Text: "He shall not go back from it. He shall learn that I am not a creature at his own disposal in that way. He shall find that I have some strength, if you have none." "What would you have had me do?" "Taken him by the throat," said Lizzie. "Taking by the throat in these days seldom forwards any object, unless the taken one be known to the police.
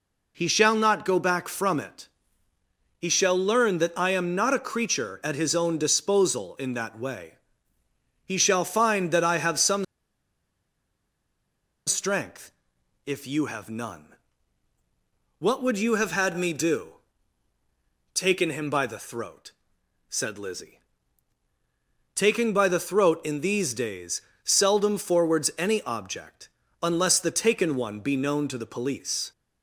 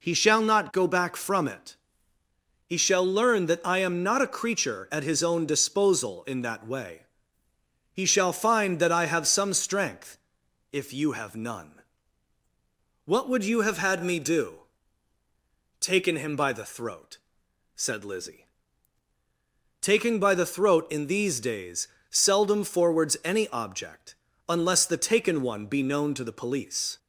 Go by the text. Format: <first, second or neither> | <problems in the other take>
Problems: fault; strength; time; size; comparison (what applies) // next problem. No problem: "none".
second | pauses between "some" and "strength"; strong; at 9.8 s; 2.0 s long // pauses between "days" and "seldom"; slight; at 24.2 s; 0.22 s long; slight in the second